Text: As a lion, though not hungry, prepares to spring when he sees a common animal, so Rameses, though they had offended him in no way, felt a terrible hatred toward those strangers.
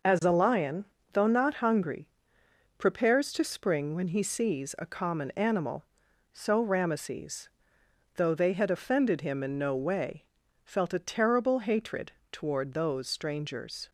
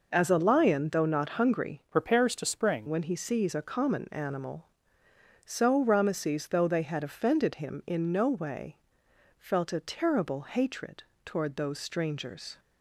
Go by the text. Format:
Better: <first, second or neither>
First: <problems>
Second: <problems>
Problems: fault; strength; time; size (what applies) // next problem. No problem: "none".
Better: first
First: pauses between "hatred" and "toward"; slight; at 12.1 s; 0.20 s long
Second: changes voice from "prepares" to "spring"; from 1.9 to 2.8 s; 0.9 s long // pauses between "hatred" and "toward"; slight; at 11.0 s; 0.20 s long